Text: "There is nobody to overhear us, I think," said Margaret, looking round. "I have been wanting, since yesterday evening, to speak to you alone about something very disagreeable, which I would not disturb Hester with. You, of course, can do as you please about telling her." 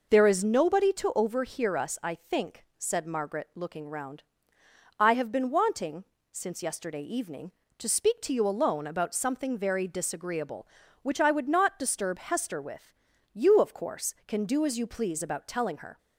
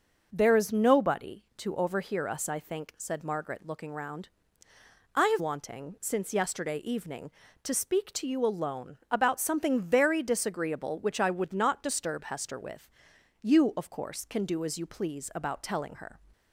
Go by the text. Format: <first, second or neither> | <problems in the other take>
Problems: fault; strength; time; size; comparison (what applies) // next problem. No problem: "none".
first | skips "been"; at 5.3 s